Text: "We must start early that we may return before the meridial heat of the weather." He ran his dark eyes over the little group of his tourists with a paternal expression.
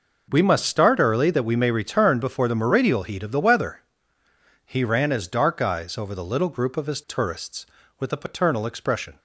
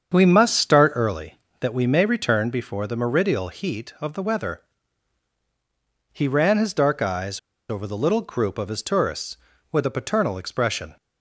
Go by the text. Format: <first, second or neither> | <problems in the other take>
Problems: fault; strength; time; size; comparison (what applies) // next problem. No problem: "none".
first | starts louder than the rest; strong; until 1.1 s; 7.5 dB // pauses between "eyes" and "over"; slight; at 7.3 s; 0.30 s long